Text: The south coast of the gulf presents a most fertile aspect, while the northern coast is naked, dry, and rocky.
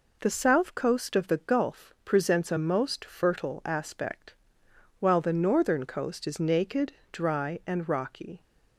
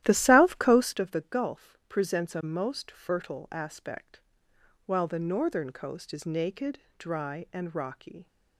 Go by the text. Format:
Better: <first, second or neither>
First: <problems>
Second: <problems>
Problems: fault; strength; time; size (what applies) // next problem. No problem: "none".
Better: first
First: none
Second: starts louder than the rest; strong; until 1.0 s; 13.5 dB